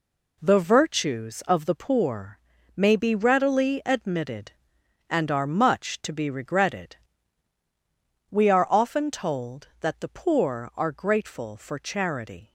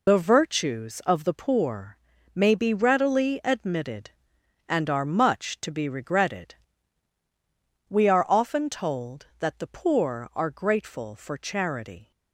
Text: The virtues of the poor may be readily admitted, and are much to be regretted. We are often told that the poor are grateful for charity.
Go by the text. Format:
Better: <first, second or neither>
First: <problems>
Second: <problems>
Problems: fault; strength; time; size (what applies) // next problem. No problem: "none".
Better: first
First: pauses between "poor" and "may"; at 2.3 s; 0.38 s long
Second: loses the start of "The"; at 0.0 s; 85 ms // pauses between "poor" and "may"; at 1.9 s; 0.38 s long